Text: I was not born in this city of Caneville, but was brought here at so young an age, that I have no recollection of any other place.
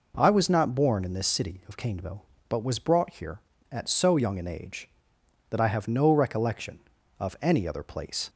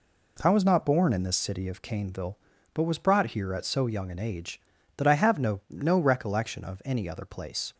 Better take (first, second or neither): first